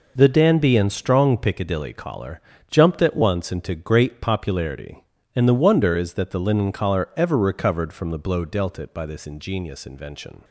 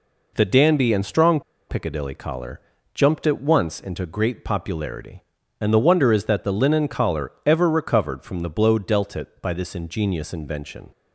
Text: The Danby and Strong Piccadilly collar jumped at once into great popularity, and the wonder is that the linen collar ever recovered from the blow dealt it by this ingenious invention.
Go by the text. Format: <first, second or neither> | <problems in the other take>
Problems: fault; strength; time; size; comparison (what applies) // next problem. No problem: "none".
first | pauses between "Strong" and "Piccadilly"; slight; at 1.4 s; 0.29 s long // pauses between "collar" and "jumped"; slight; at 2.6 s; 0.32 s long; slight in the first // pauses between "collar" and "ever"; slight; at 7.3 s; 0.16 s long